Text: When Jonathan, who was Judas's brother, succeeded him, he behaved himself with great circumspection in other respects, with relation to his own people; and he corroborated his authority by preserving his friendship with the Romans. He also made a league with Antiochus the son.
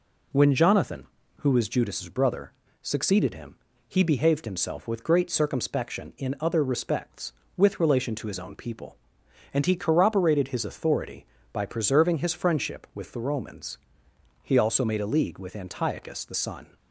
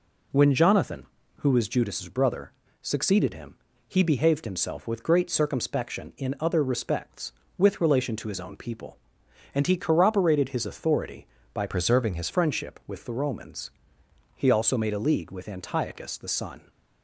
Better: first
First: none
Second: changes voice from "preserving" to "his"; from 11.6 to 12.2 s; 0.6 s long

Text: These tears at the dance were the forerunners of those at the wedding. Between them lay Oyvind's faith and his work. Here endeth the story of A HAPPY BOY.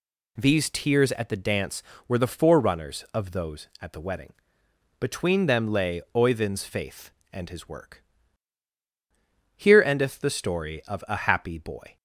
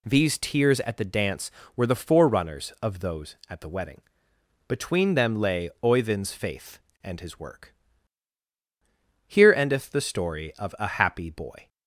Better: neither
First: none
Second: none

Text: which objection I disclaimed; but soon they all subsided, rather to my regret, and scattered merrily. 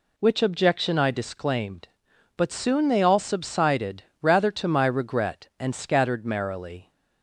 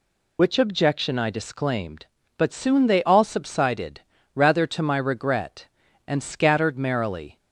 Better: first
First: none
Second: loses the start of "which"; at 0.3 s; 55 ms

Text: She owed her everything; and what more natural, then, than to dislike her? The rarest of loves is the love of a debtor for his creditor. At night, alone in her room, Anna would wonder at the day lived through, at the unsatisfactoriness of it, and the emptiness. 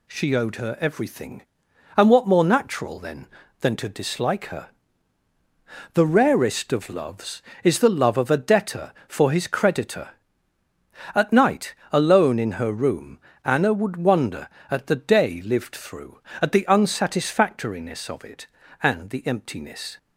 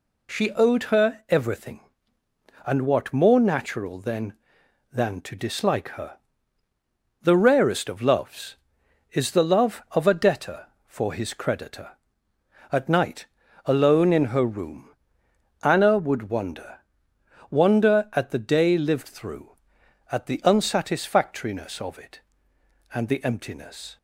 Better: first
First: none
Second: says "wonder" twice; at 17.4 s

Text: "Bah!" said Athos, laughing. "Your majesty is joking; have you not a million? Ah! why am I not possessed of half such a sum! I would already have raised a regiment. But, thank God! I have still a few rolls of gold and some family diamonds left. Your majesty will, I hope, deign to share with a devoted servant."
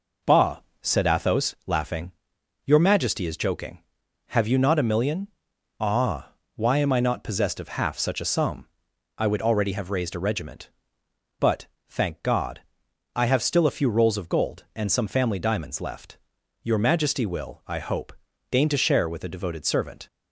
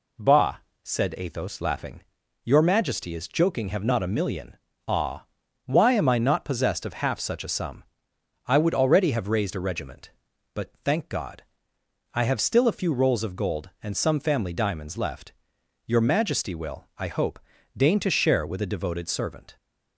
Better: first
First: none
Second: skips "you"; at 3.8 s

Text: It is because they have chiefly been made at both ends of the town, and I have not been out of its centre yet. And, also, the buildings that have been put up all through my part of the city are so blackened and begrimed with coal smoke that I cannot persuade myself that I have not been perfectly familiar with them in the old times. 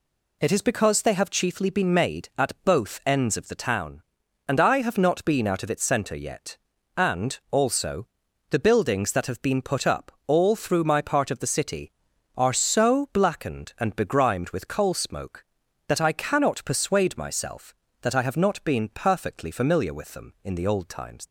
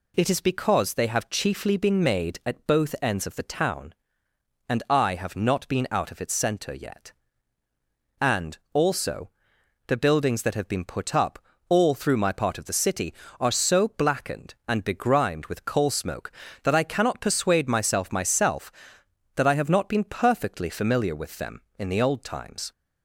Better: first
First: pauses between "up" and "all"; slight; at 10.1 s; 0.16 s long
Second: pauses between "up" and "all"; slight; at 11.3 s; 0.30 s long // says "myself" twice; at 18.1 s

